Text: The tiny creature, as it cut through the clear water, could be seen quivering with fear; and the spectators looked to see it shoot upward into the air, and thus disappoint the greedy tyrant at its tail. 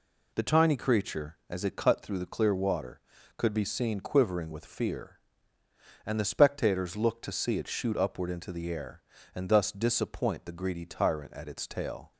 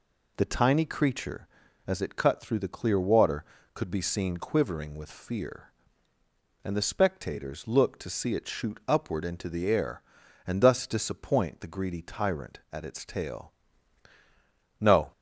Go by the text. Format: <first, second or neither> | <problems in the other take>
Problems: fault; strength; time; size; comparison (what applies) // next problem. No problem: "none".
first | goes on to say "No"; slight; from 14.7 s on; 0.32 s long